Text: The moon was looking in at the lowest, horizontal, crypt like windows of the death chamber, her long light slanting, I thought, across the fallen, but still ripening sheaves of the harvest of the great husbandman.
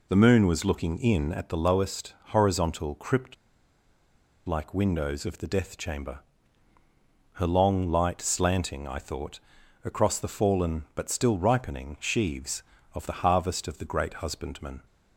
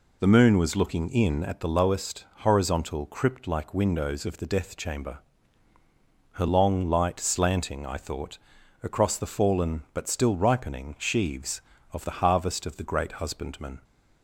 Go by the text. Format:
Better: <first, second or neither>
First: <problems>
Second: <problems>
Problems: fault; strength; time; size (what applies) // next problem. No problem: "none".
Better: second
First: pauses between "crypt" and "like"; at 3.3 s; 1.1 s long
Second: none